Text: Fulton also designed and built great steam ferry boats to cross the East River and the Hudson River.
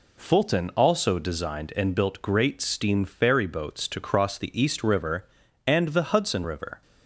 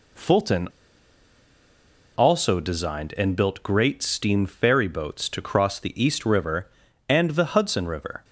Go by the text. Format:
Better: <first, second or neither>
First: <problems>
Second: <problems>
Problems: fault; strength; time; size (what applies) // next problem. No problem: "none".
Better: first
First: none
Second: pauses between "Fulton" and "also"; strong; at 0.6 s; 1.4 s long